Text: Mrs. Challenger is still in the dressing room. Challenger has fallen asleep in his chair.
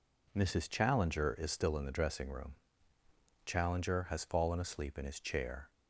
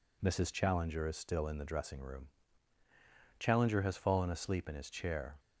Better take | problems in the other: neither | none

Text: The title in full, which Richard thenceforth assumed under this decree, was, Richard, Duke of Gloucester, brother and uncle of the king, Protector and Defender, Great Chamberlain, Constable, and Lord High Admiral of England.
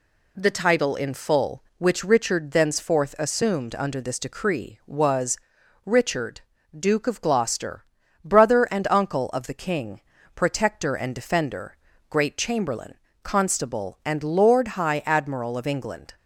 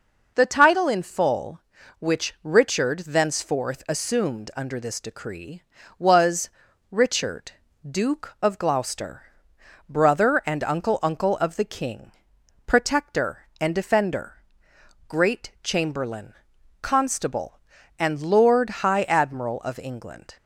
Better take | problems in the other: first | says "uncle" twice; at 11.0 s

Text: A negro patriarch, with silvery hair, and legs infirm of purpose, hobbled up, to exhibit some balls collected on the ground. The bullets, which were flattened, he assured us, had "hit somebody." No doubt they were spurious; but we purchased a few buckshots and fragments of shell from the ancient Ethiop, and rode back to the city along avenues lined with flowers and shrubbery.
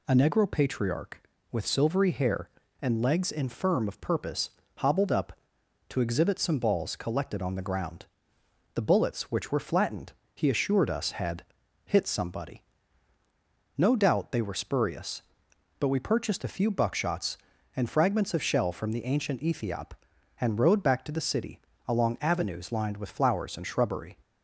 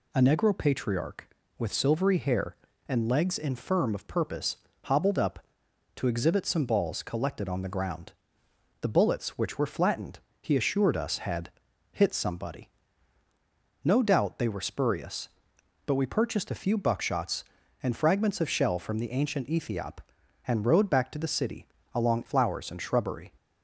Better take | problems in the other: first | pauses between "had" and "hit"; at 11.4 s; 0.42 s long; also in the first // pauses between "city" and "along"; slight; at 21.6 s; 0.26 s long; slight in the first // skips "avenues lined with"; at 22.2 s

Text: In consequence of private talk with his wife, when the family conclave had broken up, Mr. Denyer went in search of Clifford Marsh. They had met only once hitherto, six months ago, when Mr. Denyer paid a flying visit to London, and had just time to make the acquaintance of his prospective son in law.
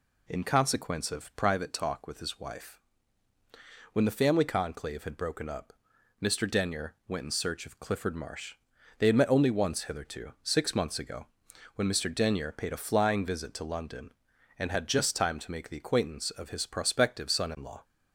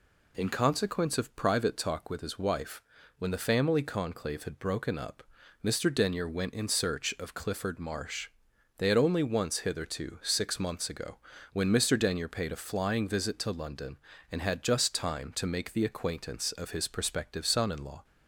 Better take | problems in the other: first | skips "met"; at 8.9 s

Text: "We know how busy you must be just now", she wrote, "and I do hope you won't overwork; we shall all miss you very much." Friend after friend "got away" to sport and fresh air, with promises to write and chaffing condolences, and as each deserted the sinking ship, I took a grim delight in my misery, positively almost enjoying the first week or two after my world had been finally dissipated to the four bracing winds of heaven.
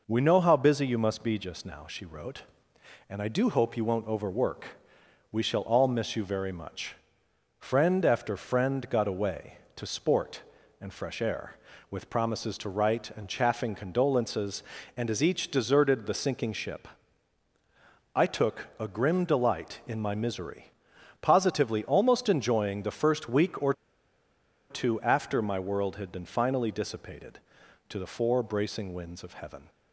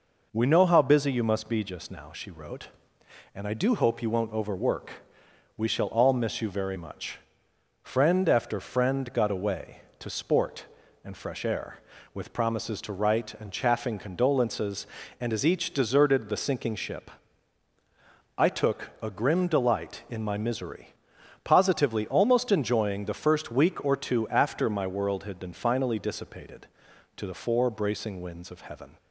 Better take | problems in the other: second | pauses between "or" and "two"; noticeable; at 23.7 s; 0.97 s long

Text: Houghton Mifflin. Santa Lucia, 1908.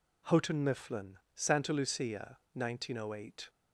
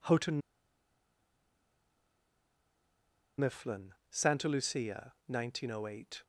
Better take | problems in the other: first | pauses between "Houghton" and "Mifflin"; strong; at 0.4 s; 2.9 s long

